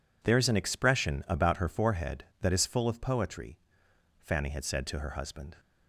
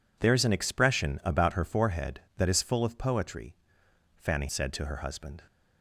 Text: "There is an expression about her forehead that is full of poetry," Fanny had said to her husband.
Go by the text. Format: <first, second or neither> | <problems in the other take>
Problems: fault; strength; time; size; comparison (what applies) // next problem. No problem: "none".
first | skips "had"; at 4.4 s